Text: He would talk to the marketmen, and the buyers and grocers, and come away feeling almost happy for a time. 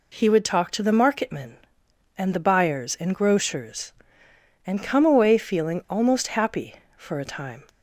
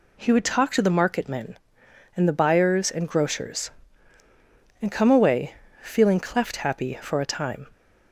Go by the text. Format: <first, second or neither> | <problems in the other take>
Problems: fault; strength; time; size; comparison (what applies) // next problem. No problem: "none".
first | pauses between "away" and "feeling"; slight; at 5.5 s; 0.30 s long // says "cleft" for "almost"; at 6.2 s